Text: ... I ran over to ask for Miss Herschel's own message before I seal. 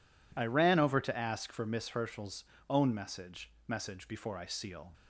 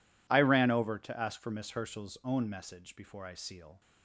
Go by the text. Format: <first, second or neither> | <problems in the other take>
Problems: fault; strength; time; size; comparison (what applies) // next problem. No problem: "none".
second | pauses between "Herschel's" and "own"; slight; at 2.4 s; 0.24 s long // says "message" twice; at 3.6 s